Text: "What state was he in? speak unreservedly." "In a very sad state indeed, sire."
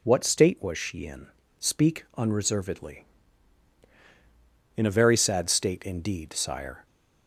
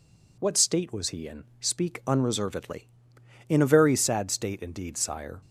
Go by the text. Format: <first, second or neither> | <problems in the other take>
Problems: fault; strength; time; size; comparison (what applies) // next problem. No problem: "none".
second | says "she" for "he"; at 0.7 s